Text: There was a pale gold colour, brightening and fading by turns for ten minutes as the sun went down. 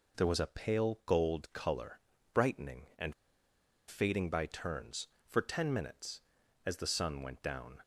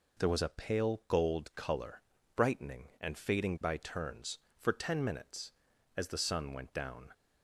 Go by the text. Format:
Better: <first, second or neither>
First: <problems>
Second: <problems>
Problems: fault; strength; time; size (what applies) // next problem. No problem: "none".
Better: second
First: pauses between "and" and "fading"; noticeable; at 3.1 s; 0.74 s long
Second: none